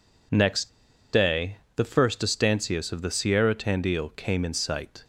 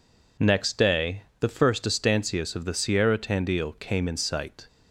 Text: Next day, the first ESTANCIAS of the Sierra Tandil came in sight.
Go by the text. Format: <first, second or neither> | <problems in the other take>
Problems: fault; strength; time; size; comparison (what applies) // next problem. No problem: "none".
second | pauses between "Next" and "day"; at 0.6 s; 0.44 s long